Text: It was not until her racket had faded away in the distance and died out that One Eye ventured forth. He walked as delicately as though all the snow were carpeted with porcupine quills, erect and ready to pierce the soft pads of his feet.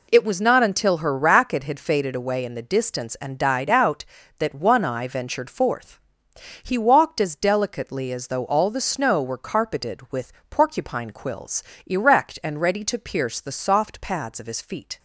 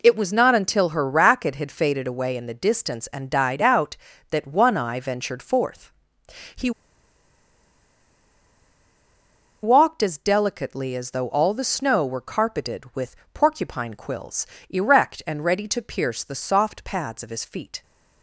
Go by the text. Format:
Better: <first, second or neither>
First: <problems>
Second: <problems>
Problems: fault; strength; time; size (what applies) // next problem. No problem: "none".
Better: first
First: pauses between "with" and "porcupine"; slight; at 10.3 s; 0.18 s long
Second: pauses between "He" and "walked"; strong; at 6.7 s; 2.9 s long // pauses between "with" and "porcupine"; slight; at 13.1 s; 0.18 s long